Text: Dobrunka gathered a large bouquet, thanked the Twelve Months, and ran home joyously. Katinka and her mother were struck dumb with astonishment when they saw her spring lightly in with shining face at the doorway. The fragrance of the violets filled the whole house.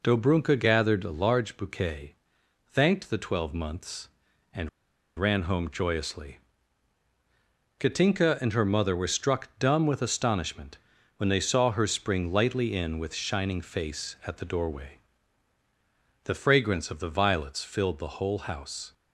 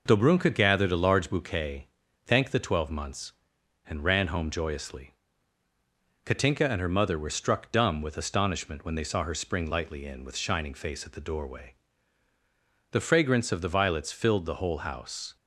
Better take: second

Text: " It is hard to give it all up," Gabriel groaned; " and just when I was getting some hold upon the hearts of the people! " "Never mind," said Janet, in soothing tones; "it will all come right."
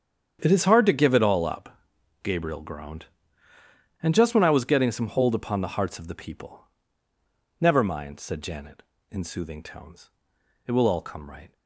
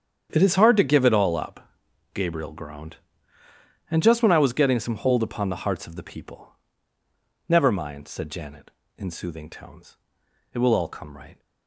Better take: neither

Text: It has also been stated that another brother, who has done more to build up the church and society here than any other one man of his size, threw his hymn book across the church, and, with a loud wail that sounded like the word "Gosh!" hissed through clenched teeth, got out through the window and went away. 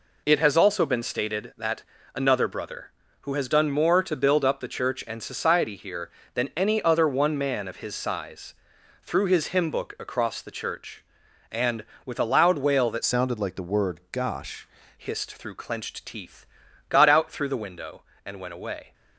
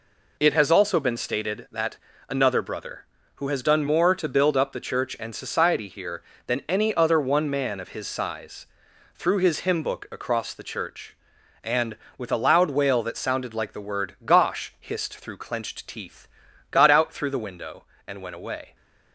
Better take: second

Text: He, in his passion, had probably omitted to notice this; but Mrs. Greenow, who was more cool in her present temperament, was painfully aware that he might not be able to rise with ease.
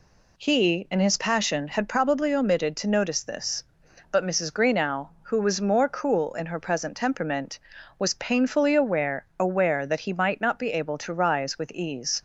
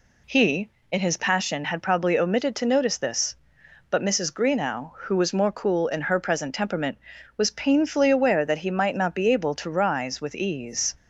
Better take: second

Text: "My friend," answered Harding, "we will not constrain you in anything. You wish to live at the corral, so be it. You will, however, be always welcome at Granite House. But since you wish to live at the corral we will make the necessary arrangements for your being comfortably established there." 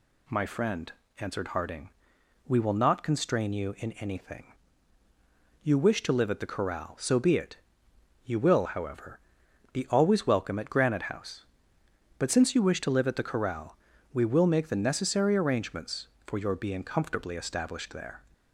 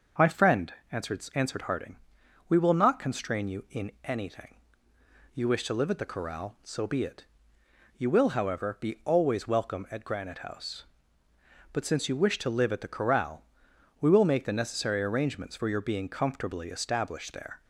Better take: first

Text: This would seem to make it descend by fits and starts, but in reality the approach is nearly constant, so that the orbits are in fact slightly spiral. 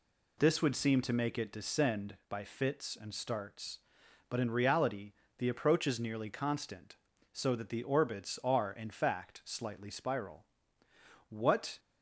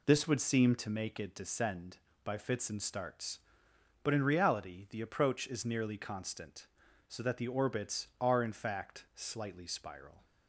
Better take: second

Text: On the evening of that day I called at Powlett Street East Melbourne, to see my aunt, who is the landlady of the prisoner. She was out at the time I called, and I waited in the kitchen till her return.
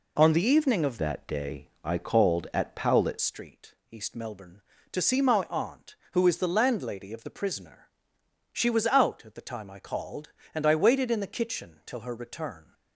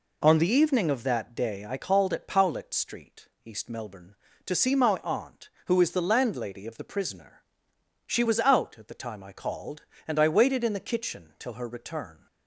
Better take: second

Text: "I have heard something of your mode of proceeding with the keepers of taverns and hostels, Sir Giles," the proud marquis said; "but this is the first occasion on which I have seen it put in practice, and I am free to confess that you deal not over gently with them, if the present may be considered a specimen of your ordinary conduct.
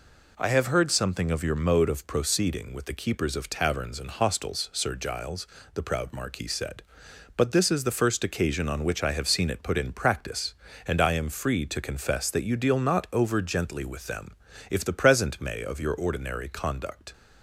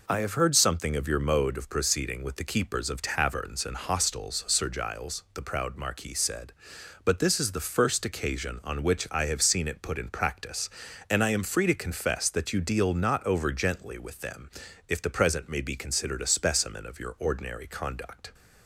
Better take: second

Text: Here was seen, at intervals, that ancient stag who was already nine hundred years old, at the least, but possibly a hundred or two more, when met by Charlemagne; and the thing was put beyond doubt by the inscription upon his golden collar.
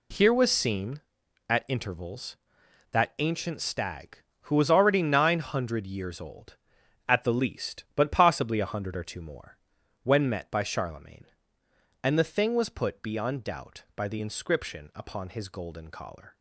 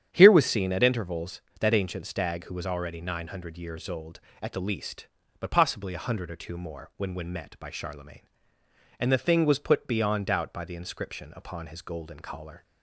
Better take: first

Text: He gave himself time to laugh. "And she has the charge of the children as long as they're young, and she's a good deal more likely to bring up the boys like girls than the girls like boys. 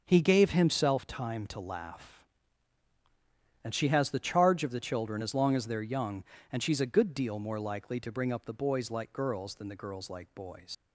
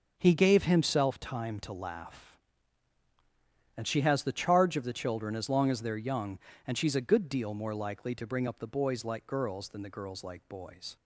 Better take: second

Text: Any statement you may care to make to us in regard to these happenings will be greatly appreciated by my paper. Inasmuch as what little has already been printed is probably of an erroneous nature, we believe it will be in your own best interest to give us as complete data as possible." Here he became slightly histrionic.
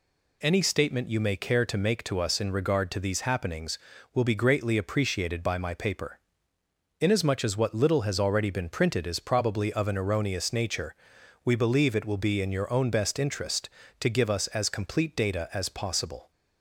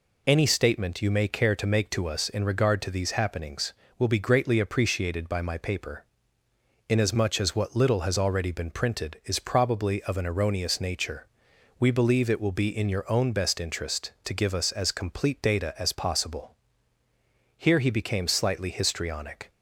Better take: second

